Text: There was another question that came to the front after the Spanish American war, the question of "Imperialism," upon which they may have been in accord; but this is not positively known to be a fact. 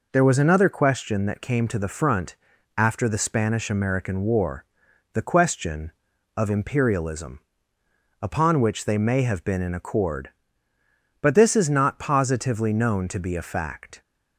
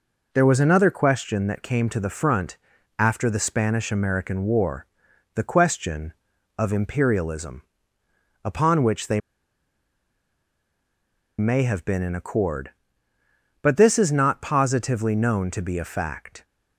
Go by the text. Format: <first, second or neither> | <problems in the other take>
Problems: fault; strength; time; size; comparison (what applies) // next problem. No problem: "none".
first | pauses between "front" and "after"; at 2.5 s; 0.40 s long; also in the first // pauses between "they" and "may"; strong; at 9.1 s; 2.1 s long